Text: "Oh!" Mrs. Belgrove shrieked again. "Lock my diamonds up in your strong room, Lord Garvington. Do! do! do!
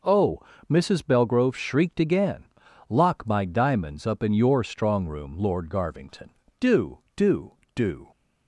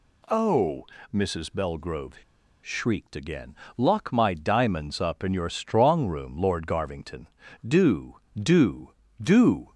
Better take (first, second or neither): first